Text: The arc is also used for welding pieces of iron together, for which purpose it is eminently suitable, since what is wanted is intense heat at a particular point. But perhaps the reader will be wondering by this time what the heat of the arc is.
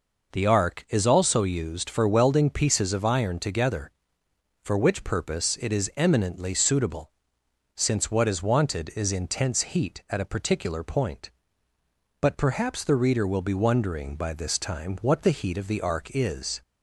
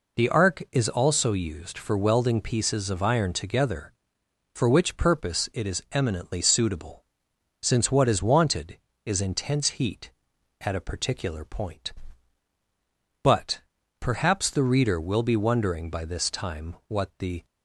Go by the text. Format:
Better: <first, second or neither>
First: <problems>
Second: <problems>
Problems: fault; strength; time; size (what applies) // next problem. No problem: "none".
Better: first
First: none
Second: pauses between "But" and "perhaps"; at 13.6 s; 0.40 s long // stops before "heat of the arc is"; at 17.4 s